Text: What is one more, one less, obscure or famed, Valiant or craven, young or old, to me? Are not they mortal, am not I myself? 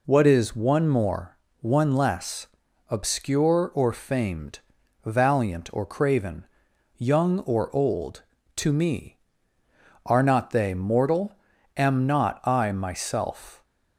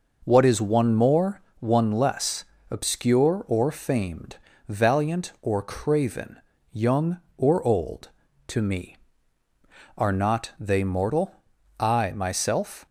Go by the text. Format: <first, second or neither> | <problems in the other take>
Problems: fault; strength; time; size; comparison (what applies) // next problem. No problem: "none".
first | skips "am not"; at 11.5 s